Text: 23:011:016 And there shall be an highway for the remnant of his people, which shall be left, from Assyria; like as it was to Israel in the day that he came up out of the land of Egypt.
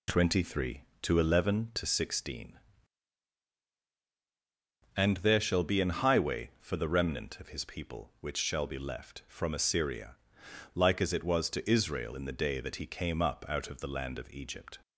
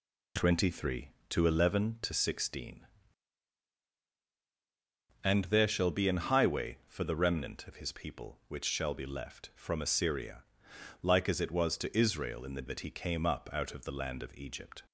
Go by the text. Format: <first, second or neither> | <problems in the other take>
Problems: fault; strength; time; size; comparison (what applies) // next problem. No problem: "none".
first | skips "day"; at 12.6 s